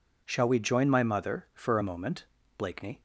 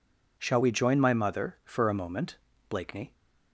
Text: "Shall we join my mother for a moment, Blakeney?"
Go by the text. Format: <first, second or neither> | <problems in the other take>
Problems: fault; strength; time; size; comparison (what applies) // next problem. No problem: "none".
neither | none